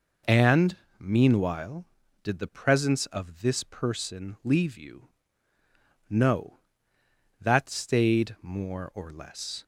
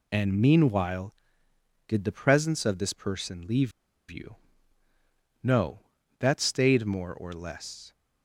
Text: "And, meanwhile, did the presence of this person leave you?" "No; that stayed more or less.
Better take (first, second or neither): first